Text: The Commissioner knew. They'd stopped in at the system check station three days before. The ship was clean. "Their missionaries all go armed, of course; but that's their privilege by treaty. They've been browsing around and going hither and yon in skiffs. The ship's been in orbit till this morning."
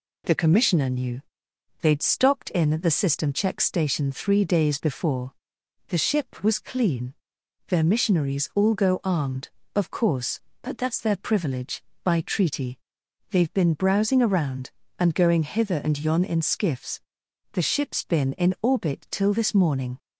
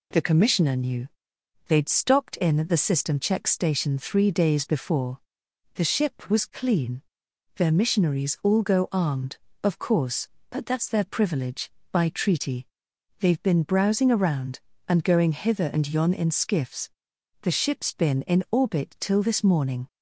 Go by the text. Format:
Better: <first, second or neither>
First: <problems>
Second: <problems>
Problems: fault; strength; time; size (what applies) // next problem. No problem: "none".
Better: neither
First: none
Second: none